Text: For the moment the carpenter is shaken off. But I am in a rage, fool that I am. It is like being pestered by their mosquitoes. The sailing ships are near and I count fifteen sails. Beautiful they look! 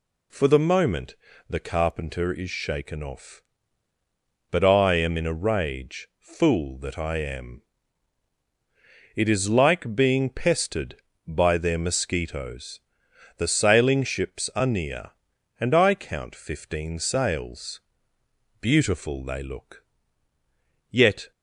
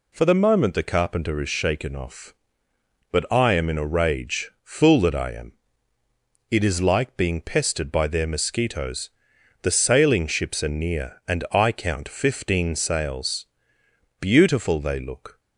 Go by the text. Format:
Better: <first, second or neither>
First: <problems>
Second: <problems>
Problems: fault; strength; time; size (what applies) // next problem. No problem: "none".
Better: second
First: pauses between "moment" and "the"; slight; at 1.1 s; 0.34 s long // goes on to say "Yet"; slight; from 20.8 s on; 0.42 s long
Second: none